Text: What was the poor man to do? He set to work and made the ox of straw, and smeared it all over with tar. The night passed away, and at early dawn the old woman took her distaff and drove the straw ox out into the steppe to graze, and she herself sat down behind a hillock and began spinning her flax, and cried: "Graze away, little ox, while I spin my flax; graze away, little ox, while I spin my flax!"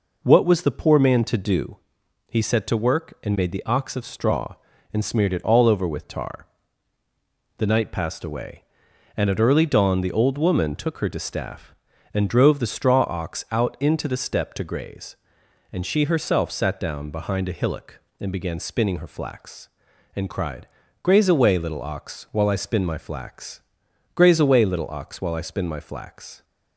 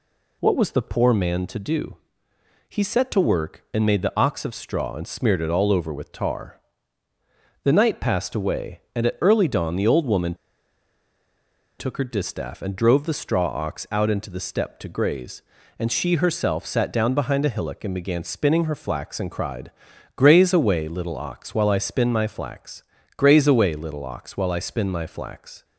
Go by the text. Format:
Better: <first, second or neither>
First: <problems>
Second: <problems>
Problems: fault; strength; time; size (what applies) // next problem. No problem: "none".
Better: first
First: none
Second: pauses between "woman" and "took"; strong; at 10.3 s; 1.4 s long